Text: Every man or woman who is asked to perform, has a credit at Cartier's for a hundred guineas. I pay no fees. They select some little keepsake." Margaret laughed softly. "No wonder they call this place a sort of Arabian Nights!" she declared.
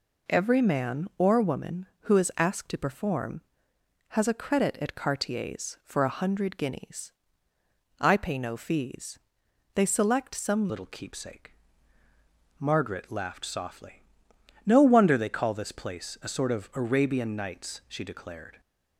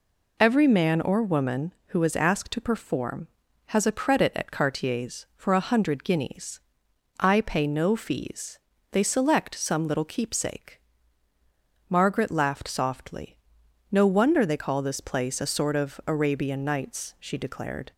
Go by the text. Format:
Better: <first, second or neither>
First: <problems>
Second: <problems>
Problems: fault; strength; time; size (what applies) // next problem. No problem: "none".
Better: second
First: changes voice at "little"; from 10.6 s on; 8.0 s long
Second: none